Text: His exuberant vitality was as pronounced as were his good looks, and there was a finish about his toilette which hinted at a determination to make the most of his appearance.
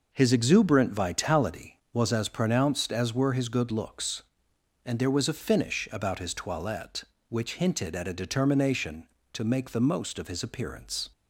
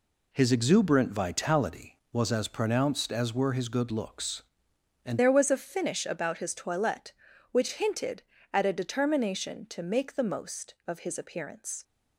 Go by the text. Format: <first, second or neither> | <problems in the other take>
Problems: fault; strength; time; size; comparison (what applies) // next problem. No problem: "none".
first | changes voice at "there"; from 5.1 s on; 6.7 s long